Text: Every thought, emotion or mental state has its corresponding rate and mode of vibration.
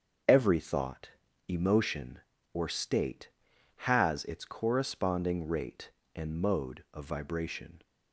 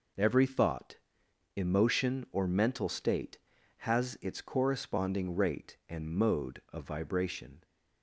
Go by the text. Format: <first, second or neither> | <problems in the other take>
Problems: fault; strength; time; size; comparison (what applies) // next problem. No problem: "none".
second | starts louder than the rest; until 1.6 s; 7 dB // skips "mental"; at 2.6 s